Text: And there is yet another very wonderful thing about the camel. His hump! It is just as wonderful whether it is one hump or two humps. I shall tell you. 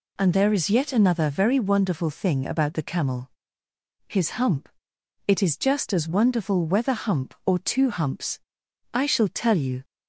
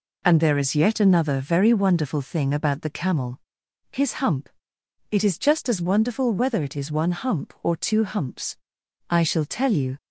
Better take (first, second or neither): second